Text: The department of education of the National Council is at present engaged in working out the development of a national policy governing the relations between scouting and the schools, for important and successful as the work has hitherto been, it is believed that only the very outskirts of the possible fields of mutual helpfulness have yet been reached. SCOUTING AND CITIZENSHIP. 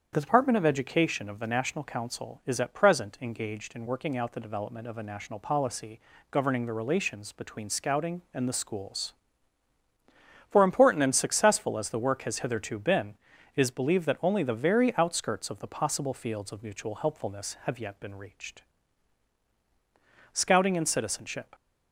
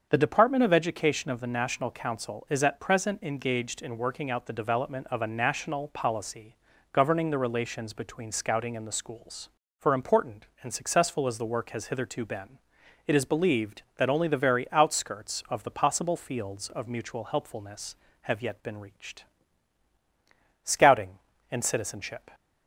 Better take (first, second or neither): neither